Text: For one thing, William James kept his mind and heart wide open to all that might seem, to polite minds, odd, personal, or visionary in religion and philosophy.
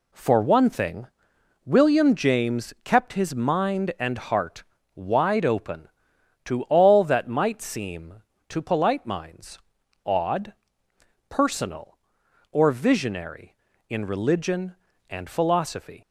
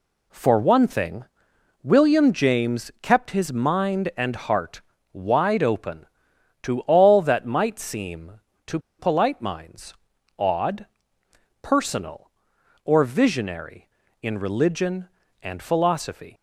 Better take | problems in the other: first | pauses between "heart" and "wide"; slight; at 4.8 s; 0.32 s long; slight in the first // pauses between "to" and "polite"; slight; at 8.7 s; 0.20 s long

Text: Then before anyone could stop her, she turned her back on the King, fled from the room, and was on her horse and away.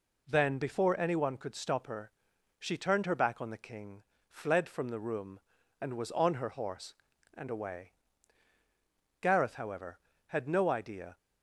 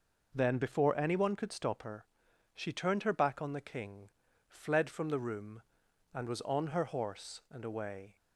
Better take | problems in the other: second | goes on to say "Gareth however had no idea"; strong; from 9.2 s on; 1.9 s long

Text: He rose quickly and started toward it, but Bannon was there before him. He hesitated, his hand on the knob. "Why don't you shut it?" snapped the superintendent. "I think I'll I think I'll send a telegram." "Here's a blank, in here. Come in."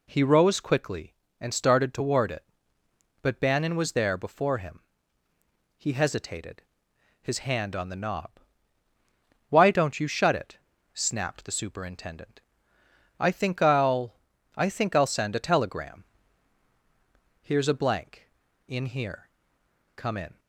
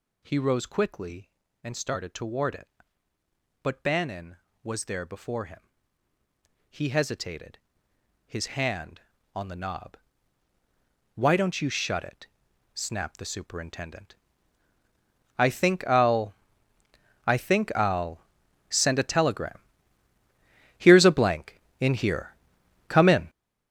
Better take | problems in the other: first | gets louder; strong; throughout; 11 dB // pauses between "I'll" and "I"; noticeable; at 16.3 s; 0.92 s long; also in the first // pauses between "I'll" and "send"; noticeable; at 18.2 s; 0.48 s long

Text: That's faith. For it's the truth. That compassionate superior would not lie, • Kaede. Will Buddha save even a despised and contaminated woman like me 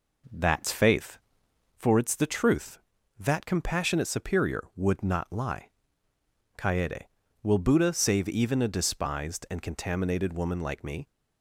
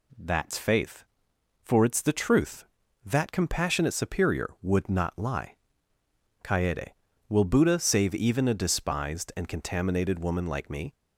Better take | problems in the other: second | starts louder than the rest; noticeable; until 1.8 s; 4 dB

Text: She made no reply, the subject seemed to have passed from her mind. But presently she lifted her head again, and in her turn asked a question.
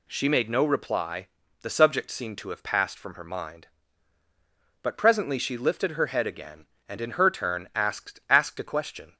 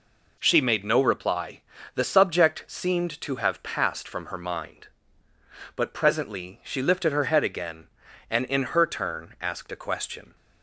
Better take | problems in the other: second | says "asked" twice; at 8.2 s

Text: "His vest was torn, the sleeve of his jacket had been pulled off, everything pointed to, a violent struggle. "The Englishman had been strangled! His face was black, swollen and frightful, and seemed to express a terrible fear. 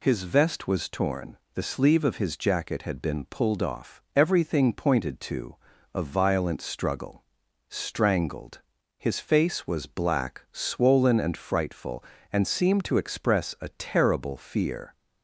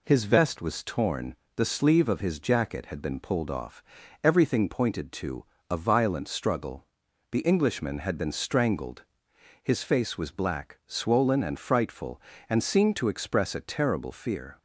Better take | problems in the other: second | skips "The Englishman had been"; at 7.4 s

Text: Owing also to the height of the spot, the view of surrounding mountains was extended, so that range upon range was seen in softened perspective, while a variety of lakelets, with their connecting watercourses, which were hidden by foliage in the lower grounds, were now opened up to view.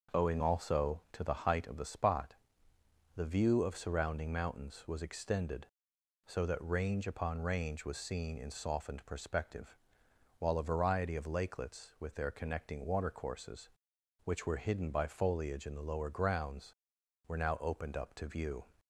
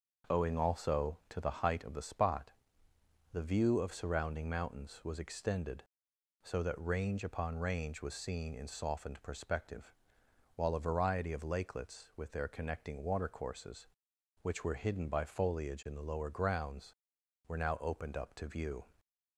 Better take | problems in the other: neither | starts louder than the rest; noticeable; the same in both

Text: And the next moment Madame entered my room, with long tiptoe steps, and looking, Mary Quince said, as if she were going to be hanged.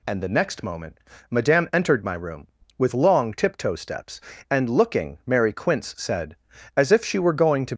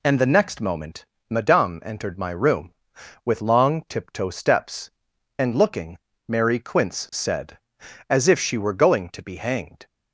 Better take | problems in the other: second | pauses between "moment" and "Madame"; slight; at 0.9 s; 0.30 s long; slight in the second // stops before "be hanged"; at 7.7 s

